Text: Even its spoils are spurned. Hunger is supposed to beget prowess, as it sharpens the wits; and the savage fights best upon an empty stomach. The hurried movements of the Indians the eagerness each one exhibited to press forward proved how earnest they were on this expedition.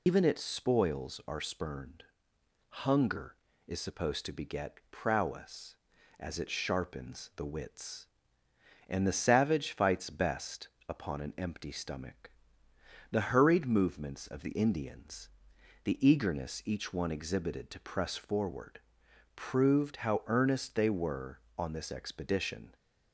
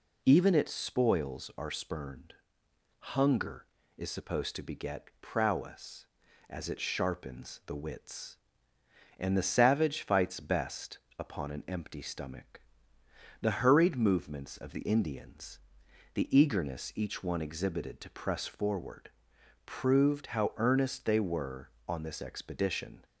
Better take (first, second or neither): second